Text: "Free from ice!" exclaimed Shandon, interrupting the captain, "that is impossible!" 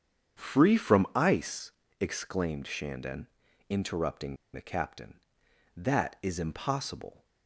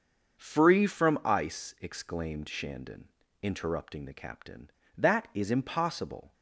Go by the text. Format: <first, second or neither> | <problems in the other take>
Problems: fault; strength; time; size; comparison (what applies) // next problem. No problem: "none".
second | starts louder than the rest; strong; until 1.4 s; 8 dB; also in the second // pauses between "interrupting" and "the"; slight; at 4.3 s; 0.17 s long